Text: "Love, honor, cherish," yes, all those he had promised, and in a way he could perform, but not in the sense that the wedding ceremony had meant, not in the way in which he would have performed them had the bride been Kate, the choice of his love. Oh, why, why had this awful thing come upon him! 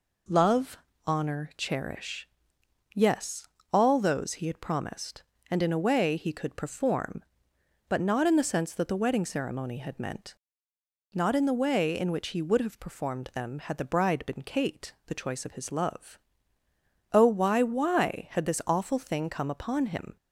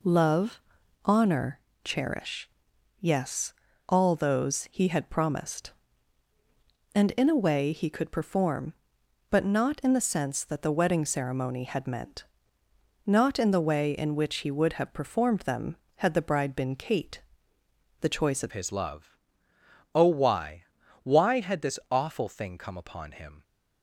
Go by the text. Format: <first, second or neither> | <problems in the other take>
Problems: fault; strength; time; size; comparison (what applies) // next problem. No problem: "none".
first | changes voice at "his"; from 18.5 s on; 4.9 s long